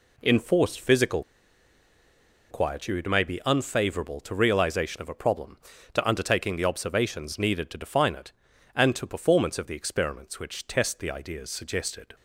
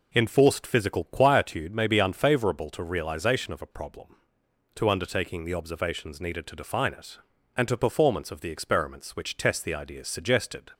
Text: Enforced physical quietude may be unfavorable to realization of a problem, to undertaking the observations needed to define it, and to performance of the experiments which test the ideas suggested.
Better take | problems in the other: second | pauses between "physical" and "quietude"; strong; at 1.2 s; 1.2 s long

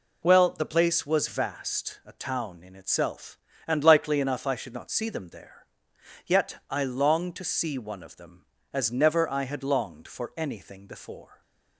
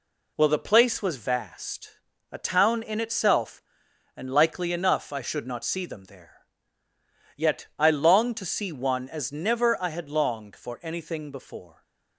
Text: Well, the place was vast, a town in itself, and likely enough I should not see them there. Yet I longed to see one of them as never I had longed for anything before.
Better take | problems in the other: first | skips "of them"; at 9.0 s

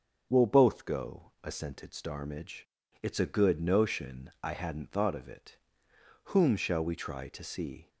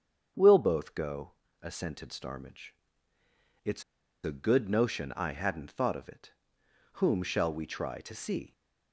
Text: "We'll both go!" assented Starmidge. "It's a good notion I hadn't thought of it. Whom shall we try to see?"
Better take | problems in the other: first | starts louder than the rest; strong; until 1.6 s; 7 dB; also in the first // pauses between "It's" and "a"; at 3.8 s; 0.42 s long

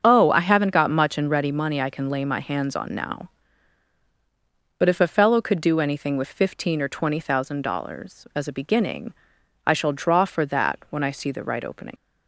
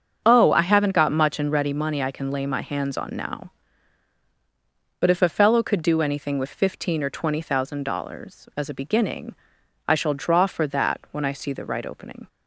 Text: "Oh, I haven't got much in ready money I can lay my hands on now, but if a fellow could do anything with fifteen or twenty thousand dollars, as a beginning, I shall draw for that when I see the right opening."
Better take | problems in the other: second | starts louder than the rest; until 1.0 s; 7 dB; strong in the second // leaves "opening" unfinished; at 11.9 s; 95 ms

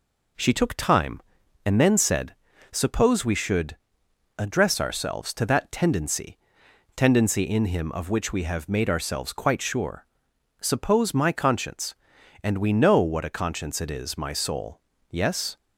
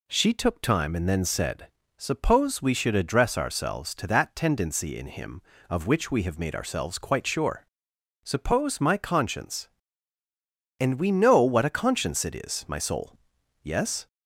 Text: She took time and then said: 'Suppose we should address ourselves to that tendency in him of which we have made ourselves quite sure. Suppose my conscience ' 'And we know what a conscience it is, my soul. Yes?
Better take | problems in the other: second | pauses between "should" and "address"; noticeable; at 3.7 s; 0.62 s long // says "tendency" twice; at 6.9 s

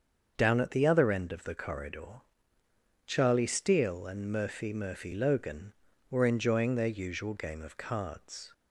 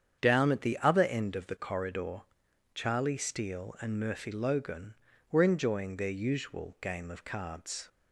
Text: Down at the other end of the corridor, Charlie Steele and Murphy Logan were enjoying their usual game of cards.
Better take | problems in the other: second | starts louder than the rest; until 1.3 s; 7 dB; strong in the second // says "Murphy" twice; at 4.7 s

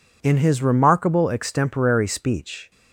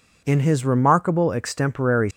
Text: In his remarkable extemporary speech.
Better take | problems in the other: first | stops before "speech"; at 2.1 s

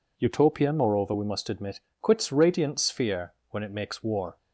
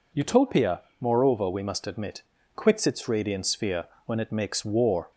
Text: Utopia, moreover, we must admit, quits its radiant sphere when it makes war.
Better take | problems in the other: second | skips "its"; at 2.3 s // pauses between "sphere" and "when"; slight; at 3.3 s; 0.18 s long; slight in the second

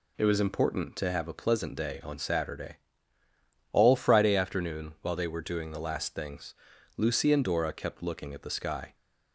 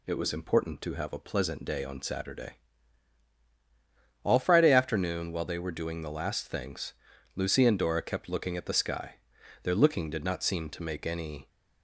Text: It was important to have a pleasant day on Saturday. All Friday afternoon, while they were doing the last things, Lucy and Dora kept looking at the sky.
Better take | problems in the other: first | goes on to say "Their looking did not seem to make any"; strong; from 9.6 s on; 1.8 s long

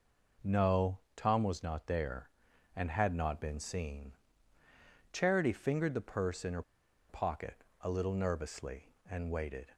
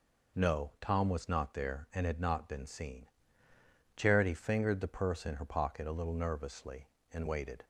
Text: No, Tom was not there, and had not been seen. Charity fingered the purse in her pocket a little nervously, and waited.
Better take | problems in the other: second | pauses between "her" and "pocket"; noticeable; at 6.6 s; 0.47 s long // pauses between "pocket" and "a"; slight; at 7.6 s; 0.18 s long

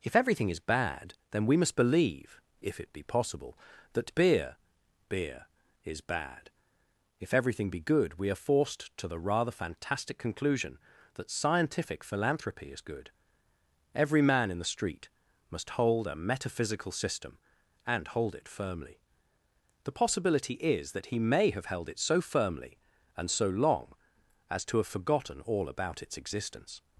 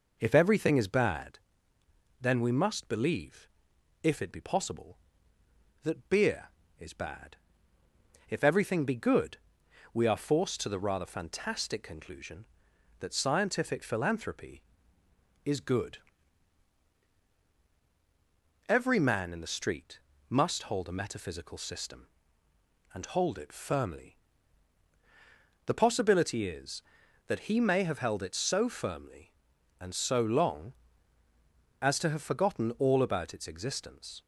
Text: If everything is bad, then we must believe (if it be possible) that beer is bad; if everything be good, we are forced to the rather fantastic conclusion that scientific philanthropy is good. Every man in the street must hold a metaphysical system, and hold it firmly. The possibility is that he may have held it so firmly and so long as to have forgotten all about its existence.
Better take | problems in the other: second | says "beer" twice; at 5.0 s // pauses between "street" and "must"; at 15.0 s; 0.42 s long; slight in the second

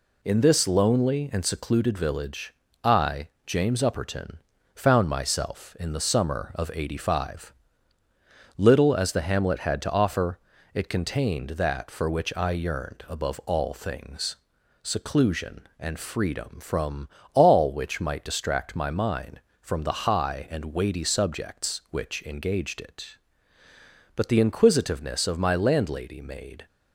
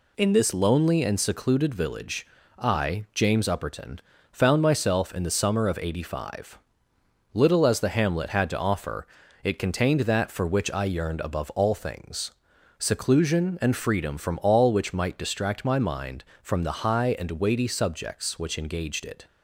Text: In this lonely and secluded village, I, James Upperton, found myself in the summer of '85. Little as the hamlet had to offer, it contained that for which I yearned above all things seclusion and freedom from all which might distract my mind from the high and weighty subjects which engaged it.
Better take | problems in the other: second | pauses between "things" and "seclusion"; noticeable; at 14.3 s; 0.46 s long; noticeable in the second // pauses between "from" and "all"; slight; at 17.0 s; 0.28 s long // goes on to say "But the inquisitiveness of my landlady made"; strong; from 24.1 s on; 2.5 s long

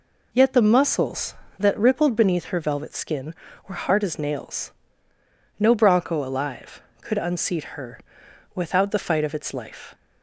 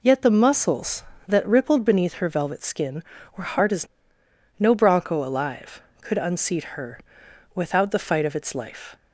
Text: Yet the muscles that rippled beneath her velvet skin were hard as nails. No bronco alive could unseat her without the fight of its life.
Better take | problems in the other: first | skips "nails"; at 4.2 s // pauses between "her" and "without"; noticeable; at 6.9 s; 0.56 s long; noticeable in the first

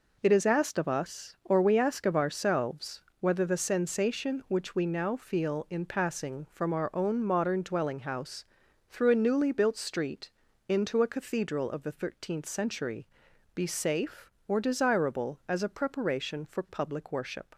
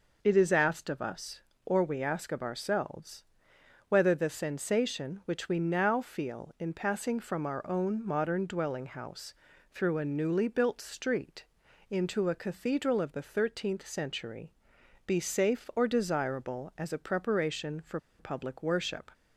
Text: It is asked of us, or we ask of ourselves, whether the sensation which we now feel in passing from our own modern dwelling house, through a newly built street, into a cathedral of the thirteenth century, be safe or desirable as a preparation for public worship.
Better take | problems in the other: first | pauses between "for" and "public"; slight; at 17.9 s; 0.20 s long

